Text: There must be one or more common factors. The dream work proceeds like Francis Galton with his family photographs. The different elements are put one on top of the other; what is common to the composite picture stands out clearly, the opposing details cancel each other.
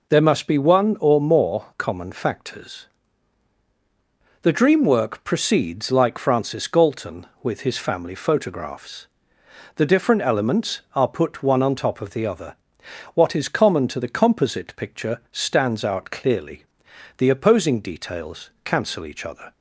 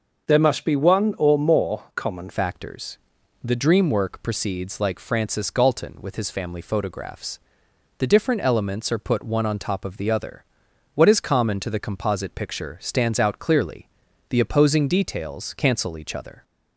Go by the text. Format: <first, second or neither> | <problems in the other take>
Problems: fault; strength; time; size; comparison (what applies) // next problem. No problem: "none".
first | starts louder than the rest; noticeable; until 1.3 s; 6 dB // changes voice at "factors"; from 2.3 s on; 14.1 s long